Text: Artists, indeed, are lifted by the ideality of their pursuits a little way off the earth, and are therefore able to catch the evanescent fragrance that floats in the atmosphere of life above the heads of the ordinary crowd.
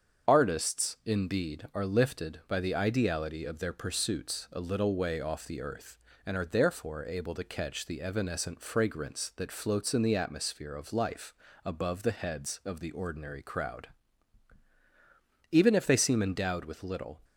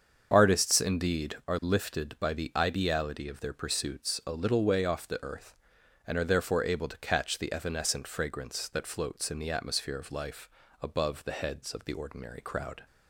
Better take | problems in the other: second | starts louder than the rest; strong; until 1.3 s; 7.5 dB; also in the second // pauses between "life" and "above"; slight; at 11.3 s; 0.30 s long; slight in the second // goes on to say "Even if they seem endowed with little"; strong; from 15.5 s on; 1.7 s long

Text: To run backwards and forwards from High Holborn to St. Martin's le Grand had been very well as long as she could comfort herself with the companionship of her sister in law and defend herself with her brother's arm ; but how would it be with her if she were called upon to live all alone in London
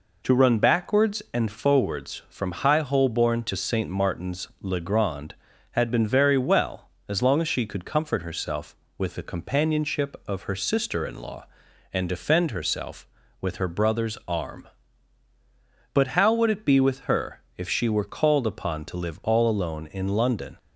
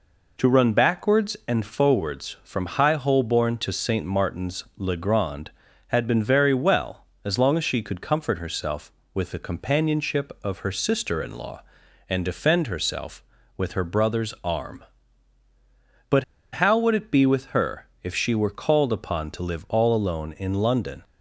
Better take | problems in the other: first | pauses between "but" and "how"; slight; at 16.2 s; 0.29 s long // pauses between "her" and "if"; slight; at 17.8 s; 0.16 s long; slight in the first

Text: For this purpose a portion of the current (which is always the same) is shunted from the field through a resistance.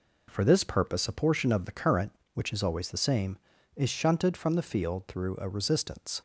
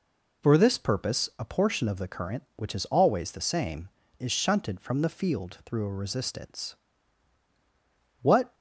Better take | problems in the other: first | goes on to say "What"; slight; from 8.2 s on; 0.32 s long

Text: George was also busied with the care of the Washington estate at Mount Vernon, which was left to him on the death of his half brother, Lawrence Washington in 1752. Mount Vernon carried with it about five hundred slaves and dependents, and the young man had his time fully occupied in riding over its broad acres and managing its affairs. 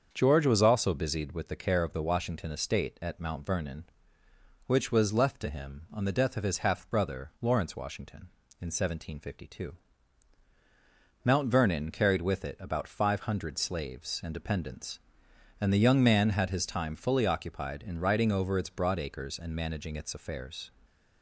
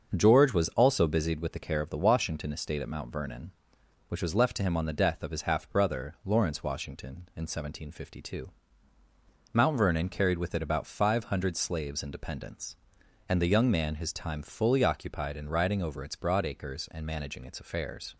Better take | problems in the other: first | starts louder than the rest; until 1.1 s; 6.5 dB; also in the first // skips "had"; at 13.9 s

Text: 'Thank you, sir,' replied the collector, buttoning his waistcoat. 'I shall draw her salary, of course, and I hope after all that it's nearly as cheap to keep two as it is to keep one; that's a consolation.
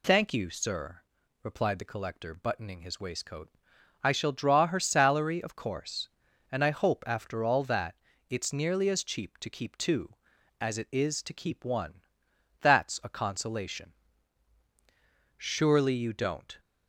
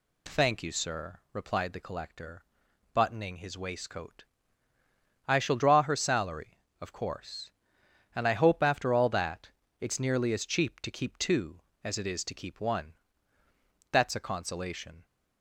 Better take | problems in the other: second | pauses between "that" and "it's"; slight; at 7.9 s; 0.34 s long; slight in the second // goes on to say "Surely you don't"; noticeable; from 15.3 s on; 1.2 s long

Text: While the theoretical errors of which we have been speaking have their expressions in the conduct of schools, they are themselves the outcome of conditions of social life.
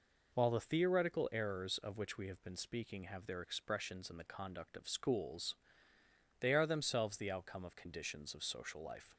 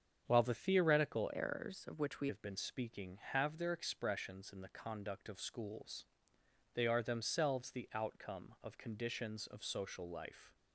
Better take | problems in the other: first | starts louder than the rest; strong; until 1.2 s; 8 dB // changes voice from "errors" to "we"; from 1.3 to 2.2 s; 0.9 s long

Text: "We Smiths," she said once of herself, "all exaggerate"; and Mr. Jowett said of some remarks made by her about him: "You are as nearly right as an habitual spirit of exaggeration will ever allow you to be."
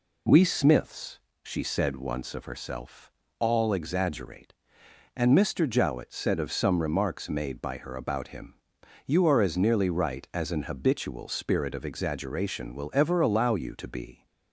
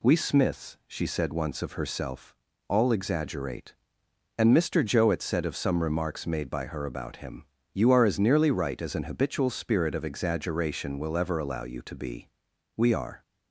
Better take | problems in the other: first | goes on to say "We are"; slight; from 12.7 s on; 0.46 s long

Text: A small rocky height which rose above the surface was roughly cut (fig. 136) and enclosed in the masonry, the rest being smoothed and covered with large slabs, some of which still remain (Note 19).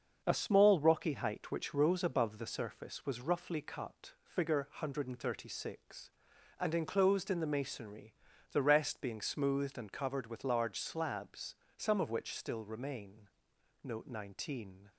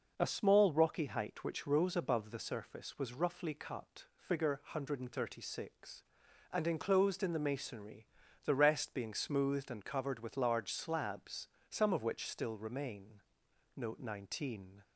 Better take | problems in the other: second | gets quieter; throughout; 6 dB

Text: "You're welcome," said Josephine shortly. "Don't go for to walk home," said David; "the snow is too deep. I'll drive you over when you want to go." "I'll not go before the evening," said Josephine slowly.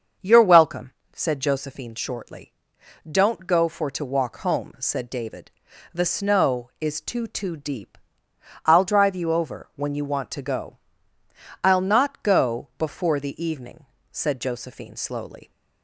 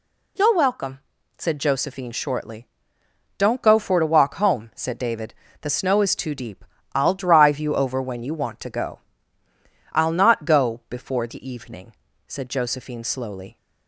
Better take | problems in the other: second | starts louder than the rest; until 1.4 s; 6.5 dB // says "too" twice; at 7.2 s

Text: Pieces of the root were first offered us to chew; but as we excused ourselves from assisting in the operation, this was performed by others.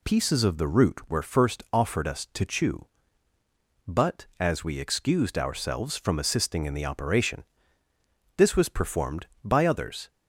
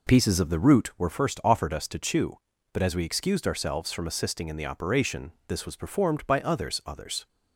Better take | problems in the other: first | says "others" twice; at 6.8 s

